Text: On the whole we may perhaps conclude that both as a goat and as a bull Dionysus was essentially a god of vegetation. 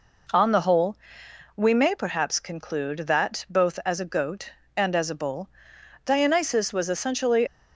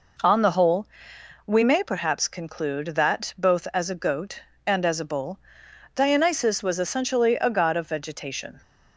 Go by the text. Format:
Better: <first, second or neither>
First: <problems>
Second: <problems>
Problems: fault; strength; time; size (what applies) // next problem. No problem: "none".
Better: second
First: pauses between "whole" and "we"; noticeable; at 0.9 s; 0.58 s long // pauses between "bull" and "Dionysus"; noticeable; at 5.4 s; 0.56 s long // stops before "a god of vegetation"; at 7.4 s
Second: pauses between "whole" and "we"; noticeable; at 0.8 s; 0.58 s long // pauses between "bull" and "Dionysus"; noticeable; at 5.3 s; 0.56 s long